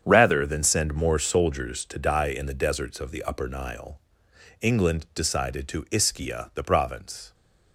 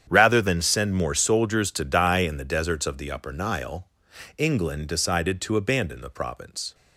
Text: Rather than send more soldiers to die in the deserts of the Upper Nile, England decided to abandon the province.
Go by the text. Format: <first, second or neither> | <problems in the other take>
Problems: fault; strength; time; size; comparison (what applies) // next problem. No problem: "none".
second | starts louder than the rest; strong; until 1.0 s; 8 dB; strong in the second // says "ischia" for "abandon"; at 5.9 s